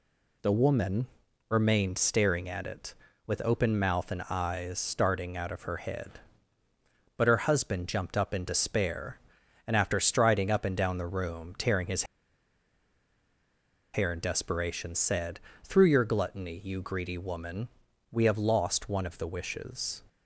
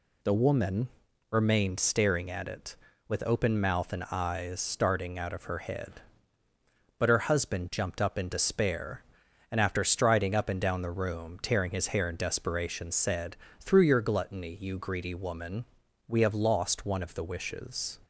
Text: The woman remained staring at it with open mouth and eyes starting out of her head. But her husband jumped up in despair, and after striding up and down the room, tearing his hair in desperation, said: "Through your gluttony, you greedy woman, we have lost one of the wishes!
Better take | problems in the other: second | pauses between "woman" and "remained"; at 1.0 s; 0.42 s long; also in the second // pauses between "his" and "hair"; strong; at 12.0 s; 1.9 s long

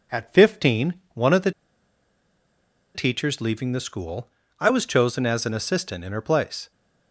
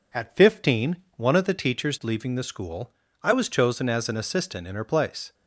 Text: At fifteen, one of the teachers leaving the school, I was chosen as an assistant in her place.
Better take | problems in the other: second | pauses between "the" and "teachers"; strong; at 1.5 s; 1.4 s long

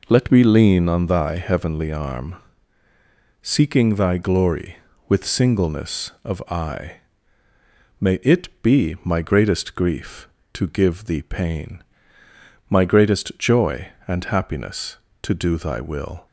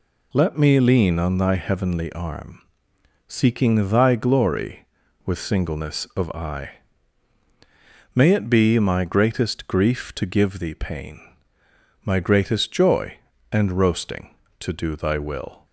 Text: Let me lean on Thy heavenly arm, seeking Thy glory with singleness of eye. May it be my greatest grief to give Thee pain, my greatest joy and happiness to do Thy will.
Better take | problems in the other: first | says "roasting" for "happiness"; at 13.7 s

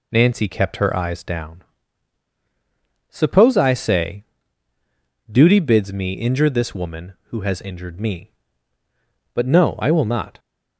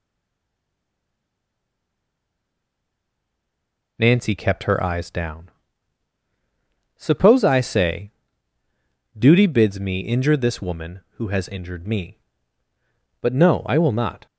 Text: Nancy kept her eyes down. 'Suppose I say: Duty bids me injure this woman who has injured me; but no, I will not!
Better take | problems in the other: first | stays silent before the first word; strong; until 3.9 s; 3.9 s long

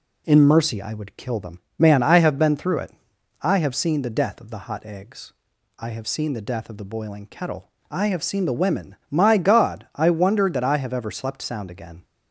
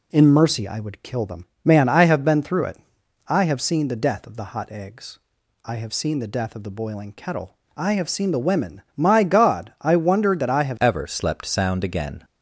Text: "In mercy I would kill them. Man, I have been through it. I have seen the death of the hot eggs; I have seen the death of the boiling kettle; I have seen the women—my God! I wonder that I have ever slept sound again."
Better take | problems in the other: first | changes voice at "ever"; from 10.8 s on; 1.4 s long

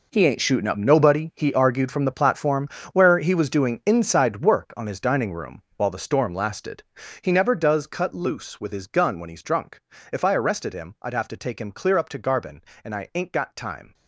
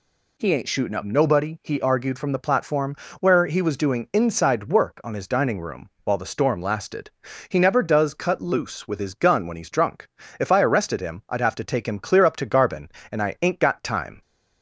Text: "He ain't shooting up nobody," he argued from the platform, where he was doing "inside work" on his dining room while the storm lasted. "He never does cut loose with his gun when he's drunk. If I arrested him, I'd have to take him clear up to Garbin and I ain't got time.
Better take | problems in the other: second | gets quieter; strong; throughout; 13.5 dB

